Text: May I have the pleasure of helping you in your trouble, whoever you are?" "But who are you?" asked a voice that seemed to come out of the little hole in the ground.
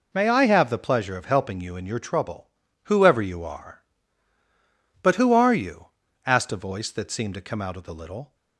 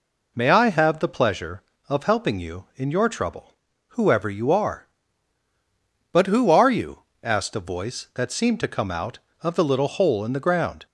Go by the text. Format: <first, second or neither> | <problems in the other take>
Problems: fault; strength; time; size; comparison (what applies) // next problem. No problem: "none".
second | stops before "hole in the ground"; at 8.3 s